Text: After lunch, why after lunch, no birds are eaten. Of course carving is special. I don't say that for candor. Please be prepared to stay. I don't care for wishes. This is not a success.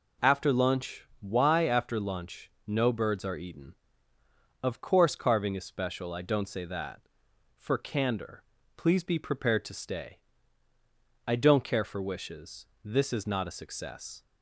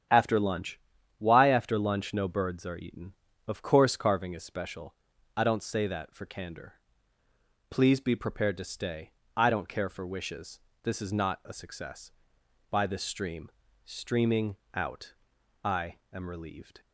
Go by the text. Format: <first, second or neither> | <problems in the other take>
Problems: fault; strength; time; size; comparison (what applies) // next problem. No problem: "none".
first | starts louder than the rest; strong; until 1.4 s; 9 dB // goes on to say "By this stream Streaming out I am relieved"; strong; from 12.6 s on; 4.1 s long